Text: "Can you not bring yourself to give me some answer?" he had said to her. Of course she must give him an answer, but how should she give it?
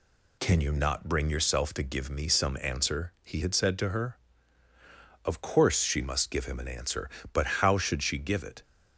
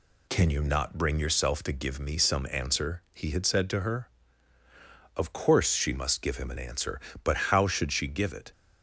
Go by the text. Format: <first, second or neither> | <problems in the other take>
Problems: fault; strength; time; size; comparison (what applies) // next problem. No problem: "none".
neither | none